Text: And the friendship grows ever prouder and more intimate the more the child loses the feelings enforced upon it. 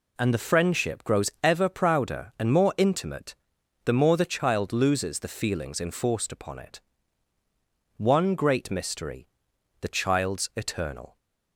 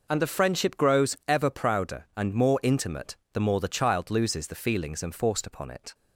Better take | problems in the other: second | pauses between "intimate" and "the"; noticeable; at 3.3 s; 0.50 s long; slight in the second // goes on to say "One great mystery the child's eternal"; strong; from 7.9 s on; 3.1 s long

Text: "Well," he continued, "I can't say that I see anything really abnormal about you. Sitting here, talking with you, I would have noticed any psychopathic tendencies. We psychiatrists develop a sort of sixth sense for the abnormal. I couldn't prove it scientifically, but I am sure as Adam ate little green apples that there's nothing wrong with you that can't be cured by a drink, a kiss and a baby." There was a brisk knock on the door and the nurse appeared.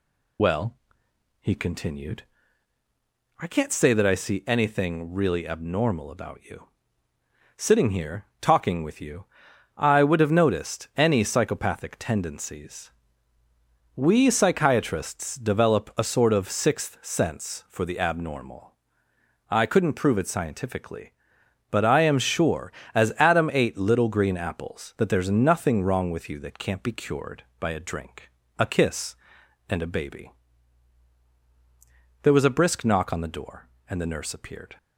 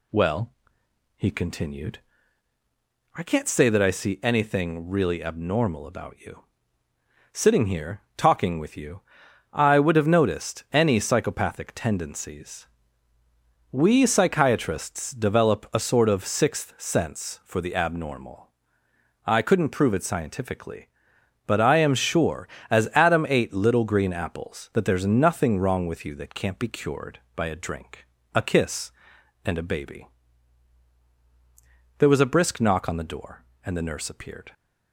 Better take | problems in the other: second | loses the start of "Well"; at 0.3 s; 45 ms

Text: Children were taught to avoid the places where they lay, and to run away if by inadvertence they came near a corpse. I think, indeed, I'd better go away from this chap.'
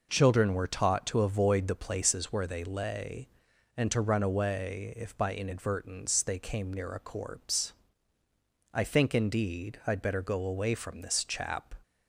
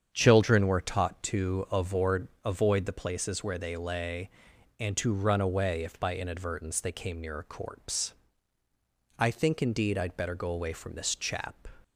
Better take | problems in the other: first | starts louder than the rest; strong; until 1.1 s; 8 dB // says "avoid" twice; at 2.4 s

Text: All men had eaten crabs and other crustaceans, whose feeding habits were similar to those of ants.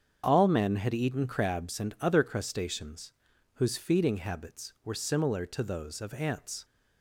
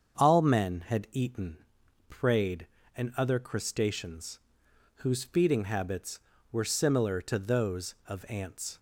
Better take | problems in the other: first | starts louder than the rest; until 1.2 s; 7 dB; strong in the first // says "prayed" for "crabs"; at 2.0 s

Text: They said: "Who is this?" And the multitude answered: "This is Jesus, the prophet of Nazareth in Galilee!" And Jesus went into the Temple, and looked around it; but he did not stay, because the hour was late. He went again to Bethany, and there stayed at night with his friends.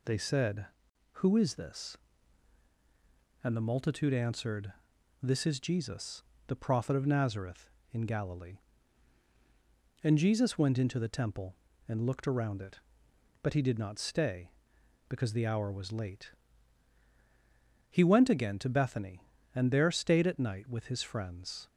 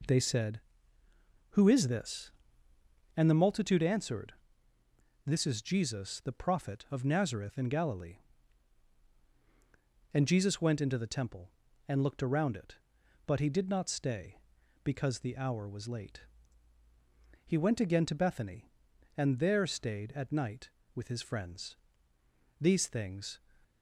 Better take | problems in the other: first | goes on to say "These things"; noticeable; from 22.5 s on; 0.80 s long

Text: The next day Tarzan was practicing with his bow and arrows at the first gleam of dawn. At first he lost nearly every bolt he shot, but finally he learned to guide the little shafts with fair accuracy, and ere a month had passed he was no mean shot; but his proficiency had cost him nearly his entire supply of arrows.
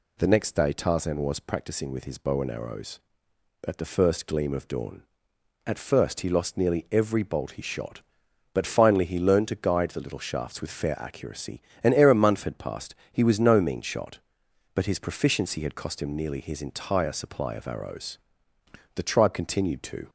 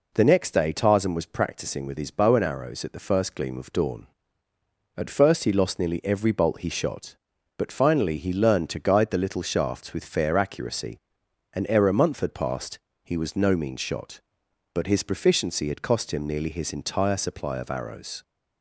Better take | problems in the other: second | pauses between "passed" and "he"; slight; at 12.9 s; 0.16 s long; slight in the second // goes on to say "The tribe continued to"; noticeable; from 18.9 s on; 1.1 s long

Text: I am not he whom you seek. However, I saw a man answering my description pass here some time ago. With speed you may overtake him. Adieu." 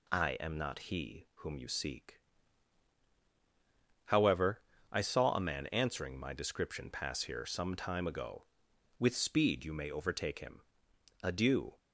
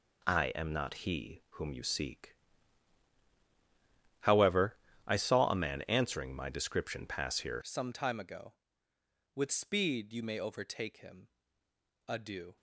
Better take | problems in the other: first | changes voice at "some"; from 7.6 s on; 4.9 s long

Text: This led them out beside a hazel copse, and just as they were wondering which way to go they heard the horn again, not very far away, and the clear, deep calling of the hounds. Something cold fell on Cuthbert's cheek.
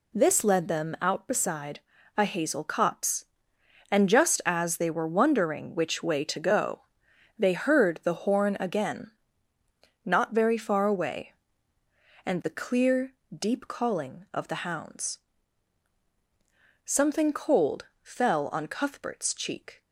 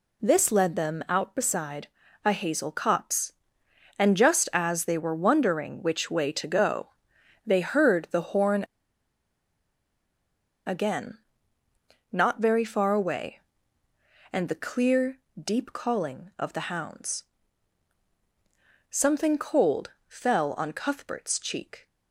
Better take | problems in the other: first | pauses between "beside" and "a"; slight; at 1.8 s; 0.36 s long; slight in the first // pauses between "go" and "they"; noticeable; at 6.8 s; 0.56 s long; noticeable in the first // pauses between "horn" and "again"; strong; at 8.6 s; 2.0 s long // pauses between "cold" and "fell"; slight; at 19.9 s; 0.18 s long; slight in the first

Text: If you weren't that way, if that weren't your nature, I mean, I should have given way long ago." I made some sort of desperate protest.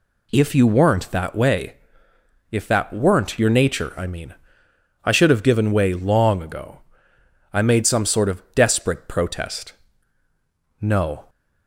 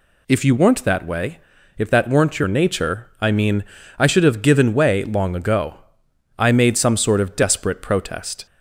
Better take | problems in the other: second | goes on to say "No"; slight; from 10.8 s on; 0.48 s long

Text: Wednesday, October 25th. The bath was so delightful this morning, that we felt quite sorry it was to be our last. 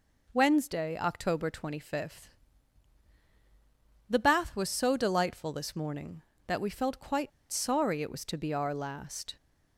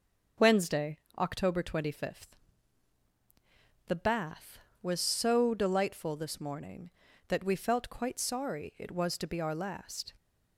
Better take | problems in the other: second | pauses between "quite" and "sorry"; slight; at 7.3 s; 0.22 s long

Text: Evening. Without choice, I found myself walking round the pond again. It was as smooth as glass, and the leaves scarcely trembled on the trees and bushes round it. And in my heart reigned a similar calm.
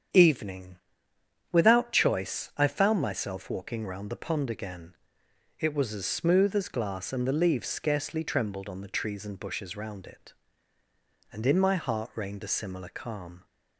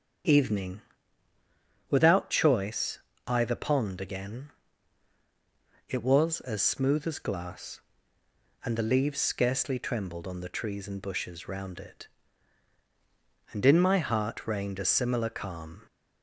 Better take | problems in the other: first | starts louder than the rest; until 2.3 s; 7 dB; strong in the first // skips "found myself walking round"; at 3.4 s

